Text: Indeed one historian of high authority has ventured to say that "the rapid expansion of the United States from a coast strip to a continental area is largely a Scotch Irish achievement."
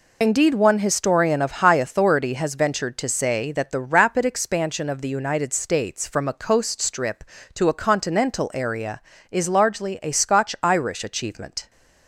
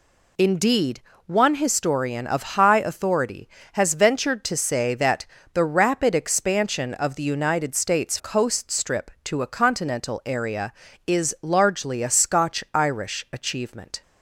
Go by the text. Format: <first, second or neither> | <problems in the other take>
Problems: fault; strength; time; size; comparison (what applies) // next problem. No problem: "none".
first | pauses between "Indeed" and "one"; slight; at 1.0 s; 0.26 s long // pauses between "that" and "the"; slight; at 5.2 s; 0.28 s long // skips "from a"; at 8.1 s